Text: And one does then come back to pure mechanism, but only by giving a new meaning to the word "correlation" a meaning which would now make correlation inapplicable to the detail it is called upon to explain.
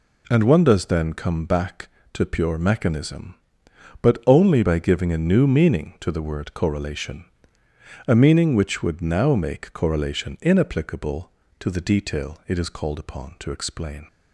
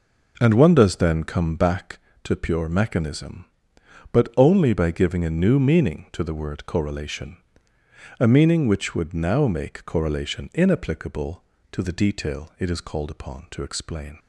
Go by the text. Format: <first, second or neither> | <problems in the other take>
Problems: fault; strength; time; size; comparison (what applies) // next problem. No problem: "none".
first | starts louder than the rest; noticeable; until 1.9 s; 5 dB // pauses between "correlation" and "a"; noticeable; at 7.3 s; 0.82 s long; noticeable in the first